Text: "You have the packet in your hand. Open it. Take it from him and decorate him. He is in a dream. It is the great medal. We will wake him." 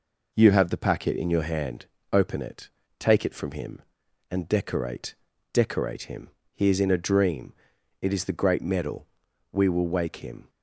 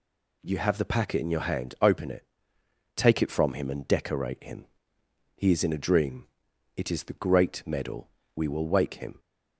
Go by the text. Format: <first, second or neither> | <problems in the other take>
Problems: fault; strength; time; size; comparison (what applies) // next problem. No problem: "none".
second | says "decorate" twice; at 5.5 s